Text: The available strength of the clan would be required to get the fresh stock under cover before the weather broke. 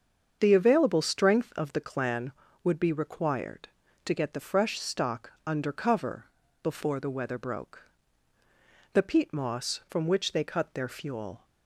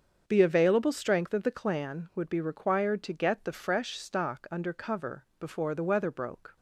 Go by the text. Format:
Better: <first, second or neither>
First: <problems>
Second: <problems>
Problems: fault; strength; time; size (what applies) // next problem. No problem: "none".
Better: second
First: starts louder than the rest; until 1.4 s; 7 dB // pauses between "stock" and "under"; slight; at 5.3 s; 0.16 s long // pauses between "cover" and "before"; slight; at 6.2 s; 0.36 s long // goes on to say "The peat moss from which they cut their fuel"; strong; from 8.9 s on; 2.5 s long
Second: starts louder than the rest; until 1.2 s; 7 dB